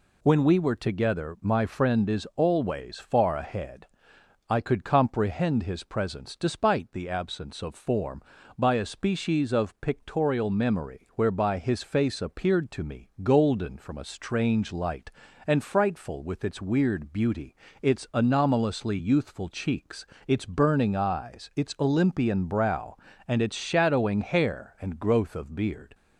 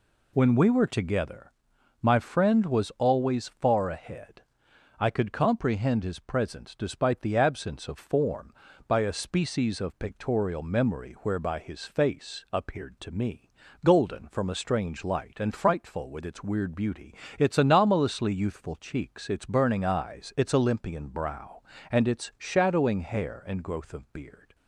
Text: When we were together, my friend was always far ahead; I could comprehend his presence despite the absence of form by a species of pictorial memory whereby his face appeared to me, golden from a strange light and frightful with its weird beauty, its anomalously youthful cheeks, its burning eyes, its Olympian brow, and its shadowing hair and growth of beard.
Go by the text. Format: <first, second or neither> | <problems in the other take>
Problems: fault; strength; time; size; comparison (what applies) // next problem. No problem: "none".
second | says "is" for "was"; at 2.0 s